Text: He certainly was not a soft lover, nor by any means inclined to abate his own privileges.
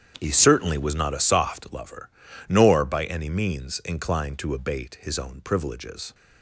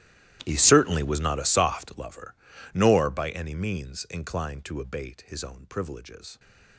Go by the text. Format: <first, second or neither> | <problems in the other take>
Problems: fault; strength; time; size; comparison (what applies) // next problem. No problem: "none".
first | gets quieter; strong; throughout; 20 dB // starts louder than the rest; strong; until 1.4 s; 13.5 dB; strong in the first